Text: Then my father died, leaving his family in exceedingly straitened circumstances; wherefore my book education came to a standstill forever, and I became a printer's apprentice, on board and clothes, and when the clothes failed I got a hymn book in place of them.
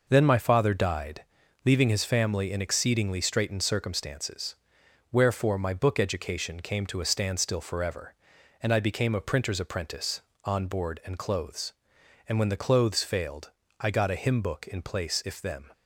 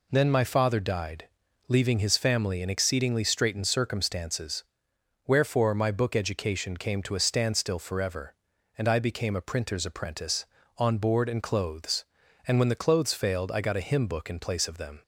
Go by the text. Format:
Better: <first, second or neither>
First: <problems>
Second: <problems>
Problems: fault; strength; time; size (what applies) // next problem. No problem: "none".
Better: second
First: pauses between "failed" and "I"; slight; at 13.5 s; 0.30 s long // says "if" for "of"; at 15.2 s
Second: none